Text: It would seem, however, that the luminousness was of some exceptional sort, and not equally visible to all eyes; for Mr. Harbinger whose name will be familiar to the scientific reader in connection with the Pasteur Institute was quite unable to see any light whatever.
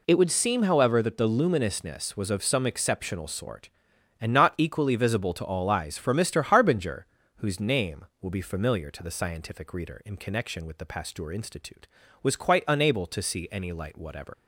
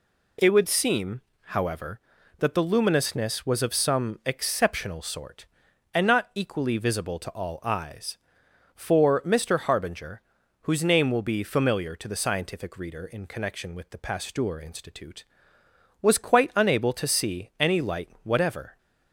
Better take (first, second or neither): second